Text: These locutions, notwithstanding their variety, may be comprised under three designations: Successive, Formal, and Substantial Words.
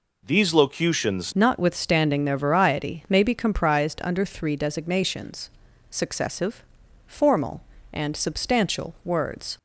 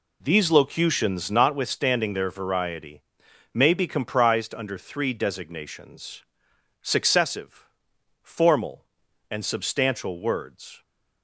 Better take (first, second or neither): second